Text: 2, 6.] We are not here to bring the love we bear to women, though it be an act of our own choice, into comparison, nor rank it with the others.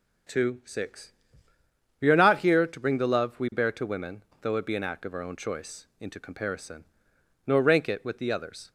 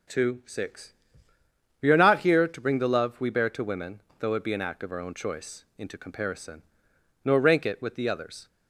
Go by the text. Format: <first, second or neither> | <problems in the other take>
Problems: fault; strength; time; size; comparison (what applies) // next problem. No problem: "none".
neither | none